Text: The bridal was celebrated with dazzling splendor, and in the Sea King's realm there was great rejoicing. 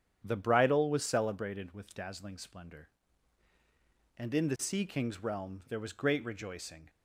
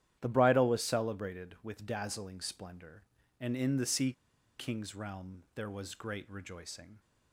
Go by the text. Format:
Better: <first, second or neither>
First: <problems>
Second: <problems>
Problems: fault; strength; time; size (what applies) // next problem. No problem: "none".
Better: first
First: starts louder than the rest; strong; until 1.2 s; 9 dB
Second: starts louder than the rest; strong; until 1.2 s; 11 dB // pauses between "Sea" and "King's"; noticeable; at 4.1 s; 0.47 s long